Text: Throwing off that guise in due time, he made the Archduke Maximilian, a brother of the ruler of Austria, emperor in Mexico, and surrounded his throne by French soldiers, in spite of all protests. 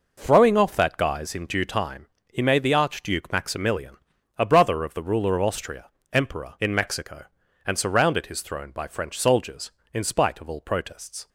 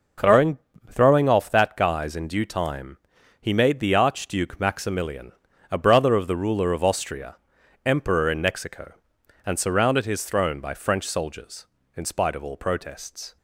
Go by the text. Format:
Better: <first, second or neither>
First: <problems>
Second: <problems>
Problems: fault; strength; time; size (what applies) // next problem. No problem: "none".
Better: first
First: none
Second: says "Throwing" twice; at 0.9 s